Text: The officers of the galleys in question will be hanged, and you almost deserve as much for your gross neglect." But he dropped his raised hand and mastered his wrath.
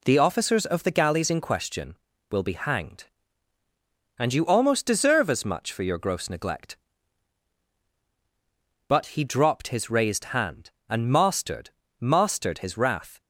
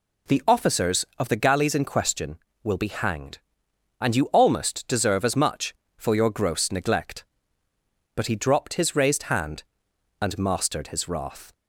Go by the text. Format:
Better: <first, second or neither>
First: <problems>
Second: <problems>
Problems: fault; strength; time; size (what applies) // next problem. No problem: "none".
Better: second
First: says "mastered" twice; at 11.9 s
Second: none